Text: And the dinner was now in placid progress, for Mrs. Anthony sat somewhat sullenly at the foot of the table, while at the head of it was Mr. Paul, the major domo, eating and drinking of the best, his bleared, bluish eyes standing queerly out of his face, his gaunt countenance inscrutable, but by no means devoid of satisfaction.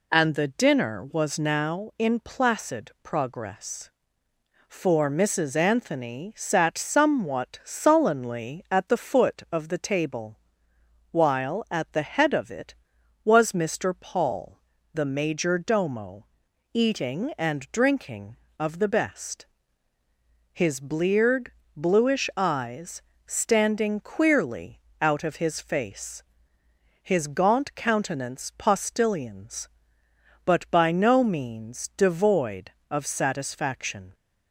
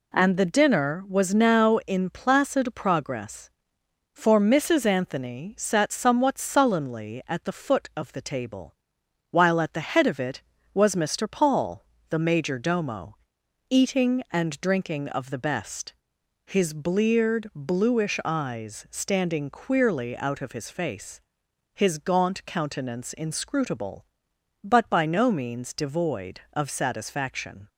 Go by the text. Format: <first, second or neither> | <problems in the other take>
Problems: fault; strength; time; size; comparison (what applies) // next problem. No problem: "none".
second | pauses between "eyes" and "standing"; slight; at 23.0 s; 0.26 s long // pauses between "queerly" and "out"; slight; at 24.7 s; 0.20 s long // says "postillions" for "inscrutable"; at 28.5 s